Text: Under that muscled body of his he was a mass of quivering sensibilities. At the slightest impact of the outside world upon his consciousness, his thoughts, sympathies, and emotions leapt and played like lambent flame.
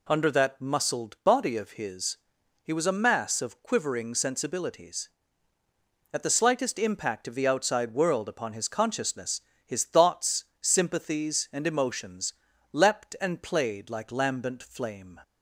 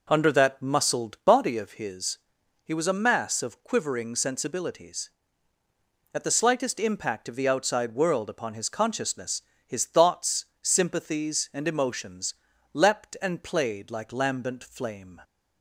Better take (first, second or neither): first